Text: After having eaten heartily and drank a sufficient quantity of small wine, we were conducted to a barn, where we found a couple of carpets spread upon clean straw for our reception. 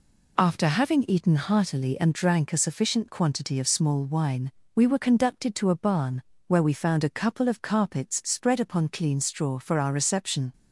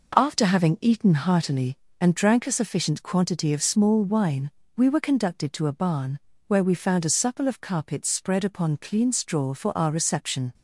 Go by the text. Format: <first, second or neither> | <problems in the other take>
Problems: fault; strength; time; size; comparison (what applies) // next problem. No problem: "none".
first | says "supple" for "couple"; at 7.0 s